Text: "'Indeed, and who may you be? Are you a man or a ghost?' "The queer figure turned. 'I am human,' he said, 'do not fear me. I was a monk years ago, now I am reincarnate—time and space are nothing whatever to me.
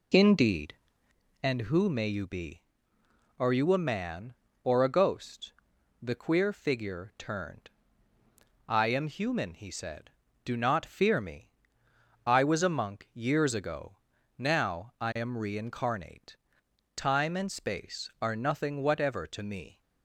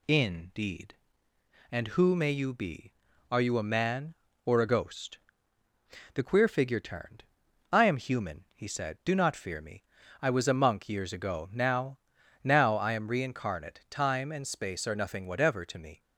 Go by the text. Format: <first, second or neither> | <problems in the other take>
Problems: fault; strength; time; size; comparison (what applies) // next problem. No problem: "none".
first | says "now" twice; at 12.4 s